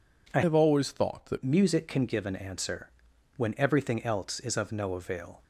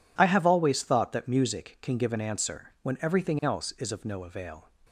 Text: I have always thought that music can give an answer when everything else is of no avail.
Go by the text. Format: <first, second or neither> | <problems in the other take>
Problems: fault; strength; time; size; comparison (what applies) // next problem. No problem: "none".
second | changes voice from "have" to "that"; from 0.4 to 1.4 s; 1.0 s long // pauses between "answer" and "when"; noticeable; at 2.9 s; 0.46 s long